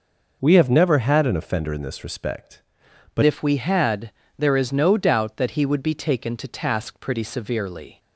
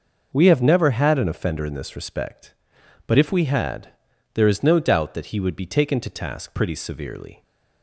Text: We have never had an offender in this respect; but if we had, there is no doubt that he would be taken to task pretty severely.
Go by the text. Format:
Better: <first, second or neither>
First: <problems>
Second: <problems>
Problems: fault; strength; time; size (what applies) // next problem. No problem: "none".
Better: second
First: changes voice at "if"; from 3.2 s on; 4.7 s long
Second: none